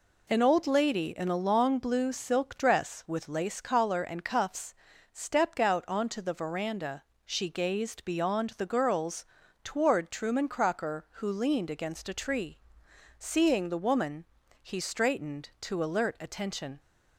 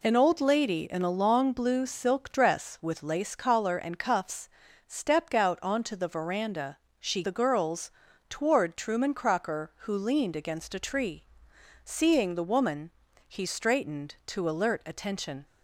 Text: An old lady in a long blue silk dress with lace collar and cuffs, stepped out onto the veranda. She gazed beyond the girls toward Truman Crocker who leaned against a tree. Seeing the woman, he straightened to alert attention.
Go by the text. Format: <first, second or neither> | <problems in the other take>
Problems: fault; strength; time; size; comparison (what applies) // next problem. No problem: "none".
first | skips "gazed beyond"; at 7.2 s // pauses between "girls" and "toward"; at 7.8 s; 0.40 s long; also in the first